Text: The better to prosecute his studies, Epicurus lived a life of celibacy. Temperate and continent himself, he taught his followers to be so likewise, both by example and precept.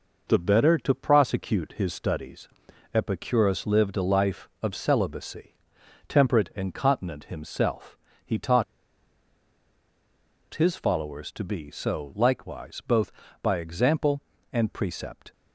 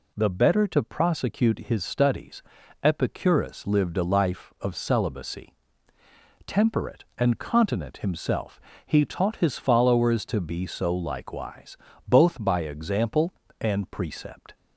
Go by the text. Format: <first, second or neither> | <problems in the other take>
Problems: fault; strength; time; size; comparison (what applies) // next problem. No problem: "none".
second | pauses between "taught" and "his"; strong; at 8.6 s; 1.8 s long